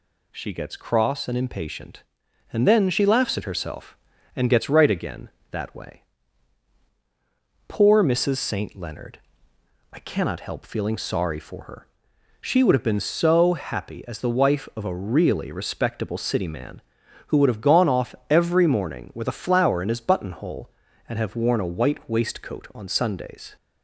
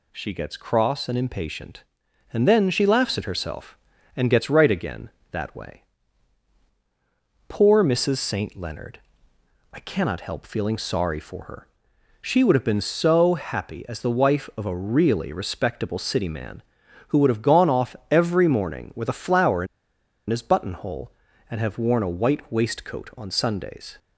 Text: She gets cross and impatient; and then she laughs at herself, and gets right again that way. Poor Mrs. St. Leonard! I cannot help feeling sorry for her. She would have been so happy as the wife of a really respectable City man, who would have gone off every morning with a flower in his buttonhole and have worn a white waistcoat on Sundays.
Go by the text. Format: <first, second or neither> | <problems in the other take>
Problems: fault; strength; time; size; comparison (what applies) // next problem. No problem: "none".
first | pauses between "in" and "his"; noticeable; at 19.6 s; 0.63 s long